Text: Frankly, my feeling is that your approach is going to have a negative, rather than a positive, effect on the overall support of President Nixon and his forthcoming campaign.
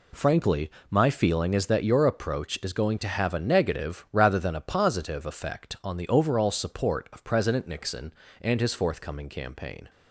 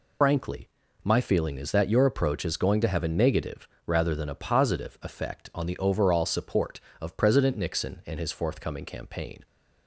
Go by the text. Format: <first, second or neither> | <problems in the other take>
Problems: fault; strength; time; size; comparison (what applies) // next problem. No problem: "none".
first | loses the start of "Frankly"; at 0.2 s; 145 ms